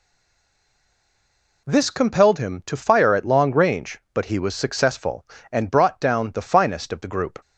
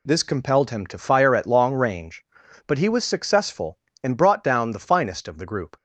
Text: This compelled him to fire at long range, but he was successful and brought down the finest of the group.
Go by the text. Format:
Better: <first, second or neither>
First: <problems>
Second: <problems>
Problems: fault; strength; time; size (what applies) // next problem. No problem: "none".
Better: second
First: stays silent before the first word; noticeable; until 1.6 s; 1.6 s long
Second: none